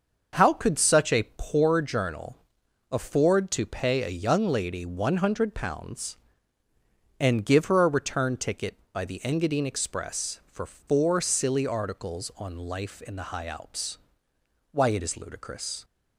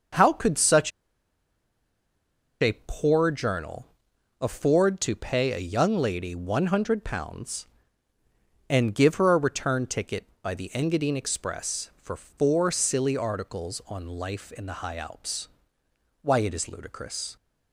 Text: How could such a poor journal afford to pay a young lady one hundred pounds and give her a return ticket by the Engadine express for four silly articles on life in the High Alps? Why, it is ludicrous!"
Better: first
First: starts louder than the rest; until 1.4 s; 6.5 dB // pauses between "journal" and "afford"; noticeable; at 2.3 s; 0.54 s long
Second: starts louder than the rest; until 2.9 s; 6.5 dB // pauses between "such" and "a"; strong; at 0.9 s; 1.7 s long // pauses between "journal" and "afford"; noticeable; at 3.8 s; 0.54 s long

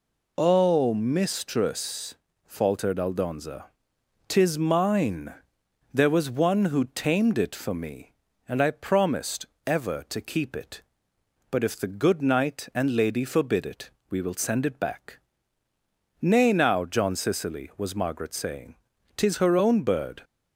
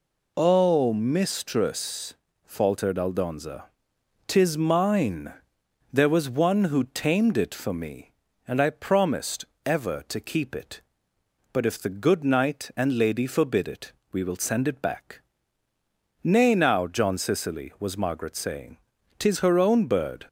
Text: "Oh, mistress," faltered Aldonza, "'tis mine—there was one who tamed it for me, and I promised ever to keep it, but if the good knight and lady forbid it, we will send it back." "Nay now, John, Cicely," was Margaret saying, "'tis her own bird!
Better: neither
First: pauses between "promised" and "ever"; slight; at 9.4 s; 0.22 s long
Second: pauses between "promised" and "ever"; slight; at 9.4 s; 0.22 s long

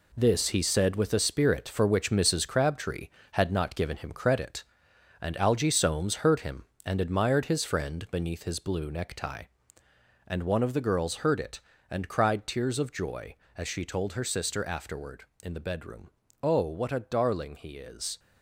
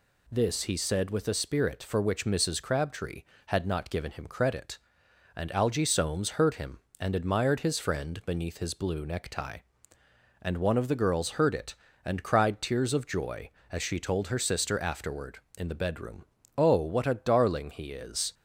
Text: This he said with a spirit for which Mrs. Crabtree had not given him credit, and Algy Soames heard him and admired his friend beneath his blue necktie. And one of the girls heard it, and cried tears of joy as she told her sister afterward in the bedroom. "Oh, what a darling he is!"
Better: second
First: gets quieter; strong; throughout; 8 dB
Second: none

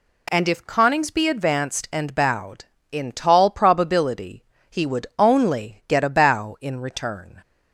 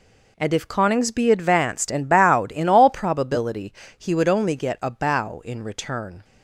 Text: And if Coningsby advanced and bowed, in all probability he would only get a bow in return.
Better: second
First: says "tall" for "all"; at 3.1 s // pauses between "probability" and "he"; slight; at 4.4 s; 0.28 s long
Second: pauses between "probability" and "he"; slight; at 3.7 s; 0.26 s long

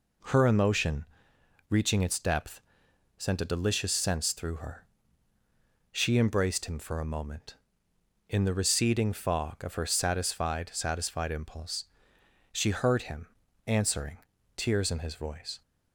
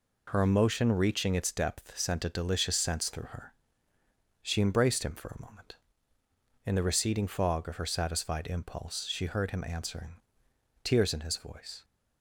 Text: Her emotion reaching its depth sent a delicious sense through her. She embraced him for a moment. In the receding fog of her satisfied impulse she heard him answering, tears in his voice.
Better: second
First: pauses between "emotion" and "reaching"; noticeable; at 1.0 s; 0.64 s long // pauses between "depth" and "sent"; noticeable; at 2.6 s; 0.56 s long // says "satisfied" twice; at 10.7 s // pauses between "impulse" and "she"; noticeable; at 11.8 s; 0.68 s long // pauses between "him" and "answering"; at 13.2 s; 0.38 s long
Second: none

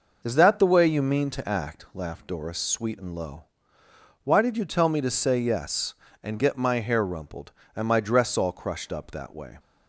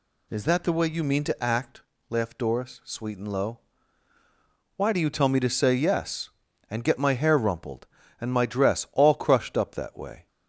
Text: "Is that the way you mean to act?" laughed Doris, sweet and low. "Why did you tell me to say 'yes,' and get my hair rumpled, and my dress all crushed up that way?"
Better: first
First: none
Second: says "do" for "did"; at 4.9 s

